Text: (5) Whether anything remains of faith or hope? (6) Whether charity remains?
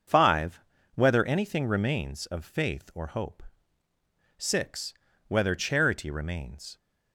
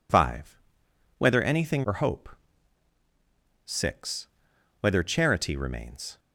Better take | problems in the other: first | skips "remains of faith"; at 1.8 s

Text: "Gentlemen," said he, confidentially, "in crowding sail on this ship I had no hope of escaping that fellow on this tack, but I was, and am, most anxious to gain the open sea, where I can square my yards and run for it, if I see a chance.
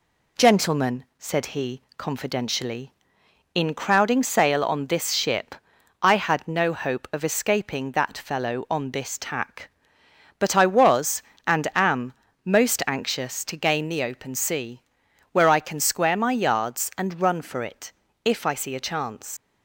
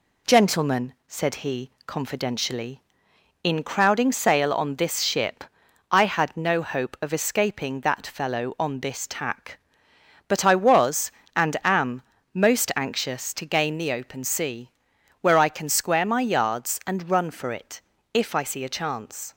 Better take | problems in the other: second | pauses between "ship" and "I"; noticeable; at 5.5 s; 0.46 s long; noticeable in the second // leaves "chance" unfinished; at 19.3 s; 85 ms

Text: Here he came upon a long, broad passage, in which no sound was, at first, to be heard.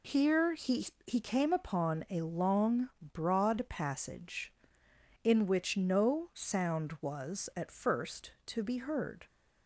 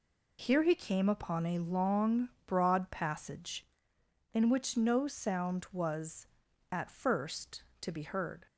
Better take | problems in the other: second | says "he" twice; at 1.0 s

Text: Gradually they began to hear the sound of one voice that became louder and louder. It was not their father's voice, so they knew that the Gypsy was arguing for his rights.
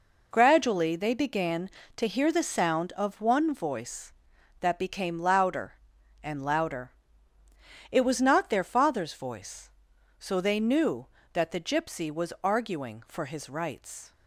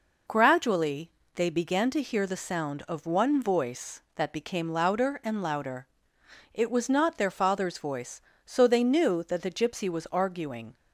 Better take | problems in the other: first | pauses between "Gradually" and "they"; slight; at 1.0 s; 0.28 s long // stops before "for his rights"; at 10.7 s

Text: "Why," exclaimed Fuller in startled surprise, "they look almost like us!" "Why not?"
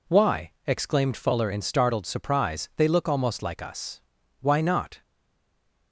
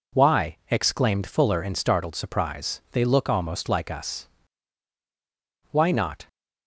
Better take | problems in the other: second | stays silent after the last word; slight; from 5.0 s on; 0.9 s long

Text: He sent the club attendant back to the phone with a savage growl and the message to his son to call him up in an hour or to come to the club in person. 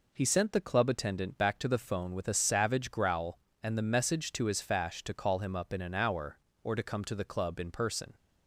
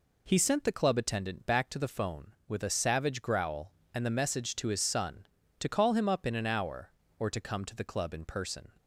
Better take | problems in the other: second | says "fash" for "son"; at 4.6 s

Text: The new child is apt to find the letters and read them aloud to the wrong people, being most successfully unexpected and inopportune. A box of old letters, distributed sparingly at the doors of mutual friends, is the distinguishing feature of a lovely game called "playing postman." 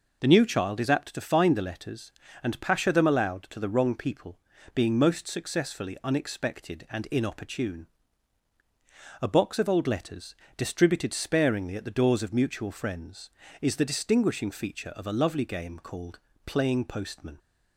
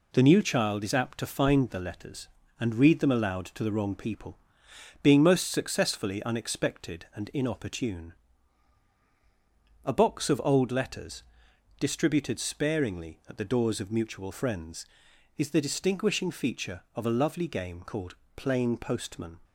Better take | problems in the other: second | says "pasha" for "read"; at 2.6 s // pauses between "called" and "playing"; slight; at 16.1 s; 0.28 s long; slight in the second

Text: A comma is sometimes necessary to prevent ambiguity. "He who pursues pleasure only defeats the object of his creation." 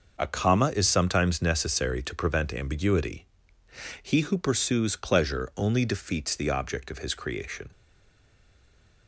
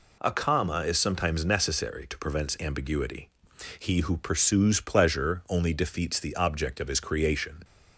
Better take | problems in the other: second | stays silent after the last word; noticeable; from 7.7 s on; 1.3 s long

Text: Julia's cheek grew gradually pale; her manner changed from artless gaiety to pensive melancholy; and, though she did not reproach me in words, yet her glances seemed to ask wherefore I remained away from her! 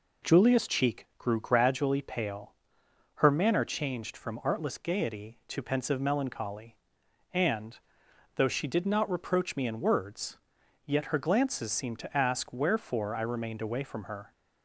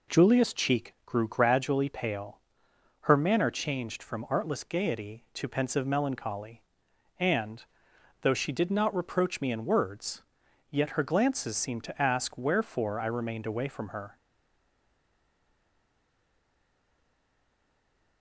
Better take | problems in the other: first | stays silent after the last word; strong; from 14.1 s on; 4.1 s long

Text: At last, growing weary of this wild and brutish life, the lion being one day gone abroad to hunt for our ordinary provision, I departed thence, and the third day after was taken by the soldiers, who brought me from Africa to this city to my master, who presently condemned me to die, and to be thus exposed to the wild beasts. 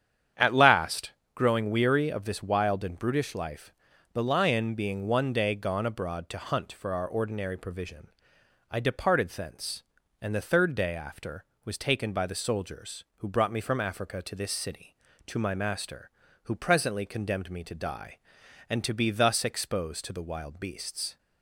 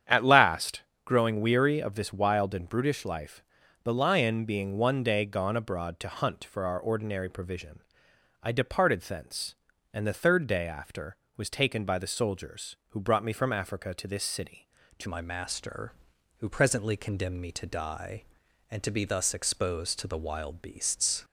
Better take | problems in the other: first | starts louder than the rest; strong; until 1.3 s; 9 dB; strong in the first // changes voice at "my"; from 15.0 s on; 6.2 s long

